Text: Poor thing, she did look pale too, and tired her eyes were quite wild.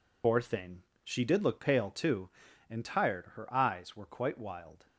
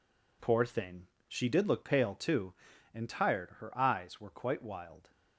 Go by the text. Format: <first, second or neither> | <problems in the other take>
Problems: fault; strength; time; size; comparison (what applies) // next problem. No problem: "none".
second | loses the start of "Poor"; at 0.2 s; 85 ms